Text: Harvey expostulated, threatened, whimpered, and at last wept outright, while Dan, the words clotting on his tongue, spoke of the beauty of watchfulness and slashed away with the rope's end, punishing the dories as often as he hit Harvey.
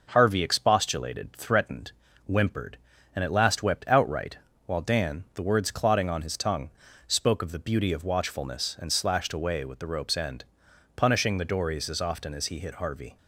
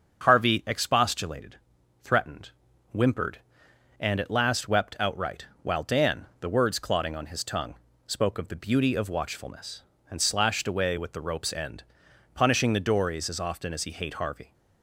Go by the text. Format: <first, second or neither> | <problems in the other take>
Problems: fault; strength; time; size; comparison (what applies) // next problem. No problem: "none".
first | starts louder than the rest; until 1.2 s; 7 dB // says "hate" for "hit"; at 13.9 s